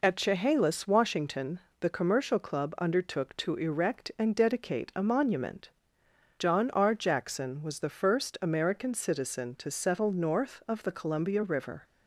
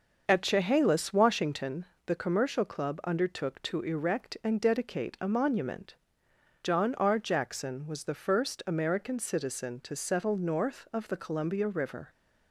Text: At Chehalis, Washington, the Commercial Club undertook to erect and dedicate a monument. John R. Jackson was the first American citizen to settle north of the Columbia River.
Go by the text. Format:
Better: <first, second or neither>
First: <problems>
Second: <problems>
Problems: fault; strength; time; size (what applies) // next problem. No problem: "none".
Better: first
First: none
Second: starts louder than the rest; until 1.8 s; 6 dB